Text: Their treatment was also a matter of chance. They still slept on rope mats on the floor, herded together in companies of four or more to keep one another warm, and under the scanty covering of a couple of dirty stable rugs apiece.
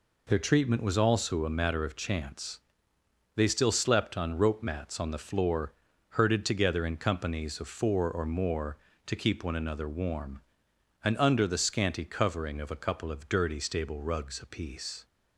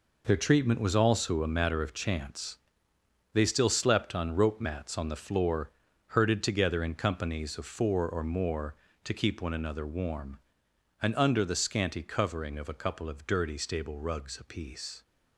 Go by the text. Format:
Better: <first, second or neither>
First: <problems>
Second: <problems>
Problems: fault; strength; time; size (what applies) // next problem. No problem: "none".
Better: first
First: none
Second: gets quieter; strong; throughout; 9.5 dB